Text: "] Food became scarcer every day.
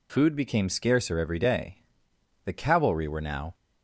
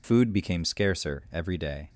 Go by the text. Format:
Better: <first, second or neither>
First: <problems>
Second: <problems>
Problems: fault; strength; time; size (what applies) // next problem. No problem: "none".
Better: second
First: goes on to say "The cavalry were now"; noticeable; from 2.4 s on; 1.1 s long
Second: none